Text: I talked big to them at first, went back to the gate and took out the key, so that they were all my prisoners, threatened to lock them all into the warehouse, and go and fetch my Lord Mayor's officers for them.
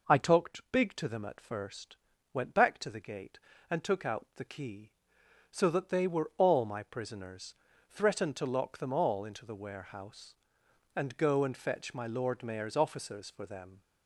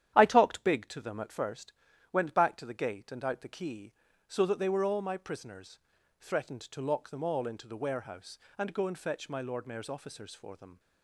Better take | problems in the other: first | starts louder than the rest; strong; until 1.1 s; 10.5 dB // skips "took"; at 3.2 s

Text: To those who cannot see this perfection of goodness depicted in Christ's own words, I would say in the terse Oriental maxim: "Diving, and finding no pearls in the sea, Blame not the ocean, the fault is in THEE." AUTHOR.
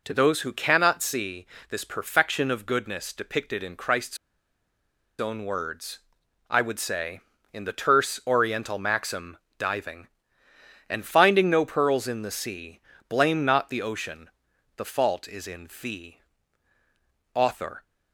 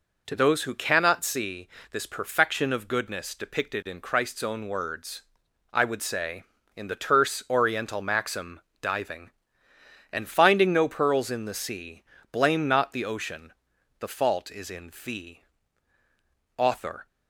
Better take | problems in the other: second | pauses between "see" and "this"; slight; at 1.4 s; 0.24 s long; slight in the second // pauses between "Christ's" and "own"; at 4.1 s; 1.0 s long

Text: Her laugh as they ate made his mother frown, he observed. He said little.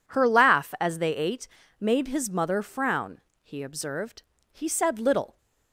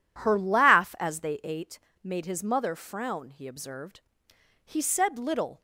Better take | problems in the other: neither | pauses between "ate" and "made"; slight; the same in both

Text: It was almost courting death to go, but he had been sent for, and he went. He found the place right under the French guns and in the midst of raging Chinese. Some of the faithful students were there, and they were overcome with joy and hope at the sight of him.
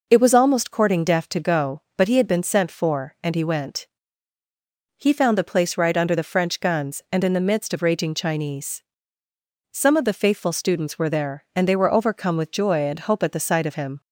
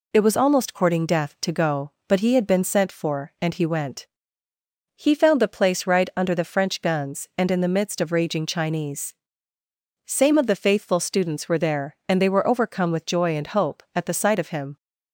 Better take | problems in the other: first | says "Same" for "Some"; at 10.0 s

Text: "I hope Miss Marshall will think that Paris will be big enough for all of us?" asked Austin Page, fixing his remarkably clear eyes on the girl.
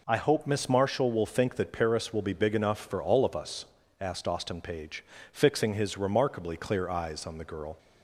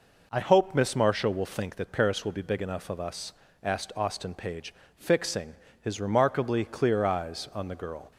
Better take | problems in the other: first | skips "for all"; at 2.9 s // pauses between "fixing" and "his"; slight; at 5.5 s; 0.26 s long

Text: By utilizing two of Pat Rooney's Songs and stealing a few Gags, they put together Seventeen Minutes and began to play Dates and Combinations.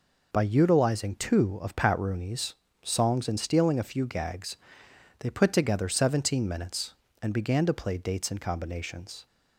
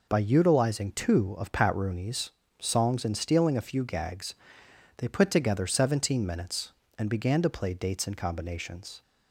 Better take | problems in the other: neither | pauses between "Rooney's" and "Songs"; slight; the same in both

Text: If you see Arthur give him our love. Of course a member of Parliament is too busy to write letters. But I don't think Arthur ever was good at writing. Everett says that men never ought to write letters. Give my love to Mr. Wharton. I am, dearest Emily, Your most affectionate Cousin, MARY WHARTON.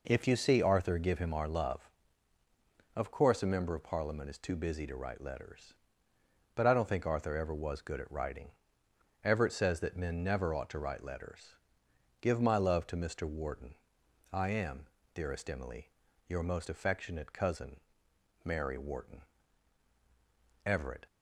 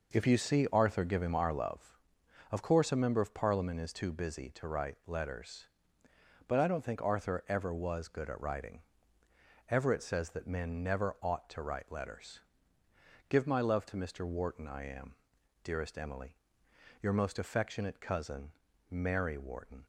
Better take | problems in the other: second | goes on to say "Everett"; slight; from 20.6 s on; 0.40 s long

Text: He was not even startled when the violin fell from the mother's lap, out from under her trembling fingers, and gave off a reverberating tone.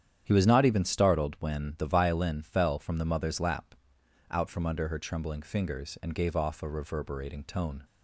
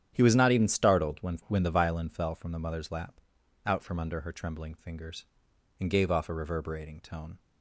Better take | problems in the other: first | starts louder than the rest; strong; until 1.1 s; 10.5 dB; strong in the first // says "when" twice; at 1.4 s

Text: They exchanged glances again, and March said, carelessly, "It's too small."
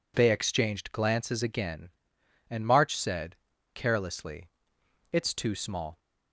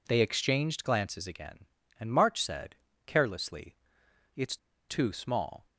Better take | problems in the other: first | pauses between "It's" and "too"; slight; at 4.5 s; 0.32 s long

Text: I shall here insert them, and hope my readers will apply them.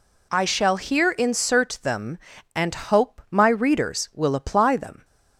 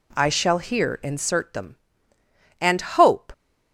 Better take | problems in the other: first | stops before "my readers will apply them"; at 3.3 s

